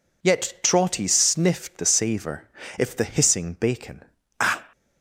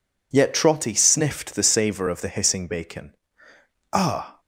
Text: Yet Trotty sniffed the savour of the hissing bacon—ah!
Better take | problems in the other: second | says "if" for "of"; at 2.7 s

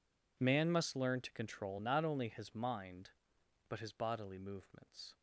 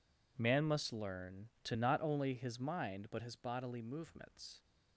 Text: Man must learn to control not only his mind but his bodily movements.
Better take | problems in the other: first | skips "control"; at 1.7 s

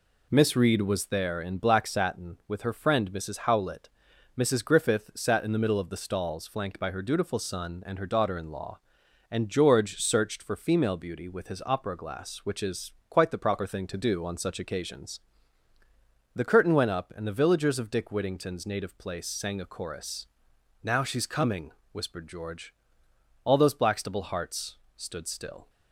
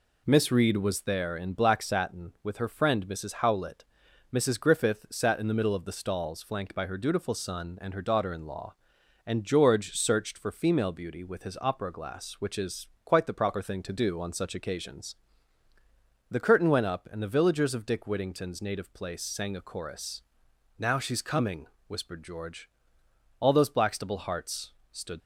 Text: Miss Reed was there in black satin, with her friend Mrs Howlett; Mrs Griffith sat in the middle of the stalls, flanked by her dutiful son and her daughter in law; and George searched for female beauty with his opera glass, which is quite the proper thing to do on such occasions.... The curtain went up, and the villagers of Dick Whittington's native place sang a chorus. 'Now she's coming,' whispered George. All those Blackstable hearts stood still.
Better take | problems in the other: first | pauses between "is" and "quite"; slight; at 12.8 s; 0.18 s long; slight in the first // pauses between "hearts" and "stood"; slight; at 24.7 s; 0.18 s long; slight in the first // stops before "still"; at 25.2 s

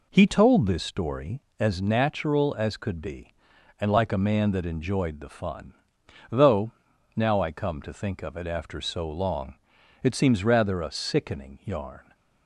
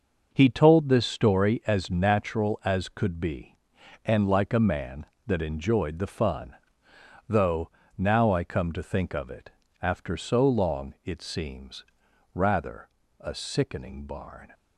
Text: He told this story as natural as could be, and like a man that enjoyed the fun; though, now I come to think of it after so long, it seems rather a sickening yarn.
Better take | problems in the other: first | pauses between "it" and "after"; slight; at 9.5 s; 0.30 s long // pauses between "seems" and "rather"; noticeable; at 11.8 s; 0.50 s long // pauses between "rather" and "a"; slight; at 12.8 s; 0.32 s long // says "barn" for "yarn"; at 14.0 s

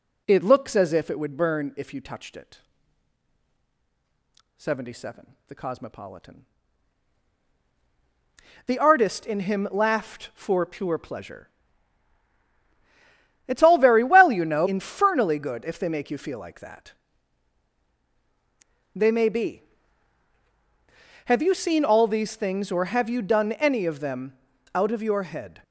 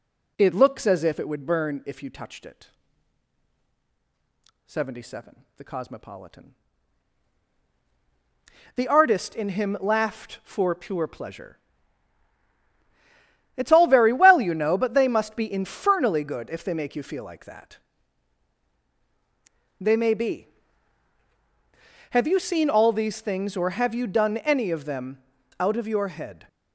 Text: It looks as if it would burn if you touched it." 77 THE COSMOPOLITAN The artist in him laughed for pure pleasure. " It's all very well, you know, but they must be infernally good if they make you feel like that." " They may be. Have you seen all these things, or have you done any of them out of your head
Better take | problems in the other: second | pauses between "COSMOPOLITAN" and "The"; strong; at 6.4 s; 2.2 s long; strong in the second // skips "but they must be"; at 14.6 s // pauses between "them" and "out"; slight; at 24.3 s; 0.36 s long; slight in the second

